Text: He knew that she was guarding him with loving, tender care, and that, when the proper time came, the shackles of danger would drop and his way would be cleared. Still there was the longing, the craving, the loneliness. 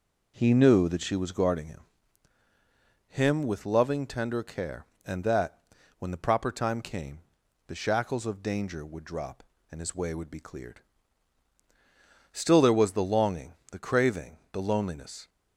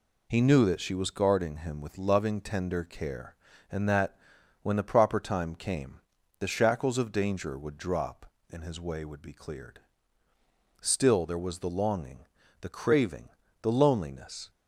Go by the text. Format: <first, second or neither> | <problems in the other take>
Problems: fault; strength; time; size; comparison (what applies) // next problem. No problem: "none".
second | says "him" twice; at 3.0 s